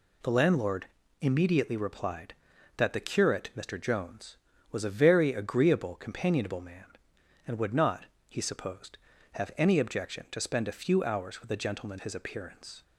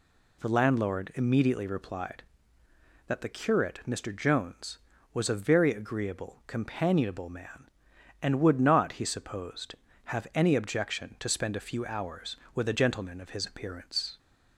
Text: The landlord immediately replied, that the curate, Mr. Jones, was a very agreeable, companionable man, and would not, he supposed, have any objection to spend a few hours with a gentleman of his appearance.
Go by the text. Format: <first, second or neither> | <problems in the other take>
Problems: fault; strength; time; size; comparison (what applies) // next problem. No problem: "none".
second | pauses between "landlord" and "immediately"; slight; at 0.8 s; 0.34 s long // skips "of"; at 12.0 s